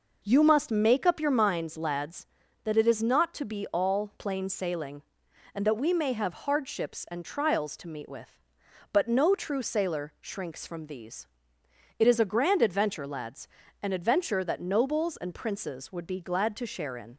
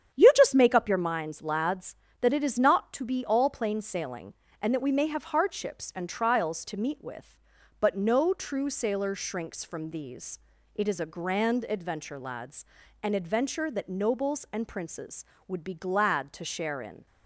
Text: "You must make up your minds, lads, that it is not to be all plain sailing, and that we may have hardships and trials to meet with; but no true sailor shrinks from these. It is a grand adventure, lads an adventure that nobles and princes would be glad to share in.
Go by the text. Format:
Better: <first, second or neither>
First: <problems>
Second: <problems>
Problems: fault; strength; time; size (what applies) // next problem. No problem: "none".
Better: first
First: pauses between "lads" and "an"; slight; at 13.4 s; 0.34 s long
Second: starts louder than the rest; strong; until 1.2 s; 9 dB // says "just" for "must"; at 0.3 s // pauses between "lads" and "an"; slight; at 12.6 s; 0.36 s long